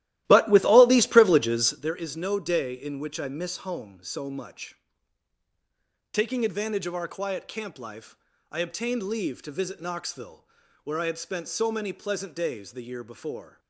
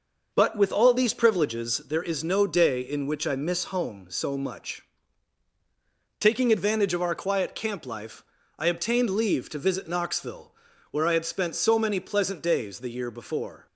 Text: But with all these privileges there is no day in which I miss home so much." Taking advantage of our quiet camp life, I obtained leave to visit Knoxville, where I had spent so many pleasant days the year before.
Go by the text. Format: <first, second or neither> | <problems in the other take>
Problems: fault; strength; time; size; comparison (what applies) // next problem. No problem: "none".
second | starts louder than the rest; strong; until 2.0 s; 14.5 dB